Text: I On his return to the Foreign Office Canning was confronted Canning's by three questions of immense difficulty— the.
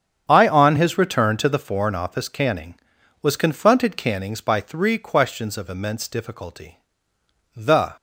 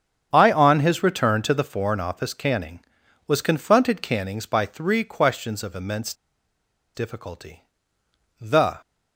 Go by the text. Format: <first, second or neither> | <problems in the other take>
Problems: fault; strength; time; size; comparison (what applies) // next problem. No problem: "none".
first | starts louder than the rest; strong; until 1.3 s; 8 dB; strong in the first // pauses between "immense" and "difficulty"; noticeable; at 6.1 s; 0.81 s long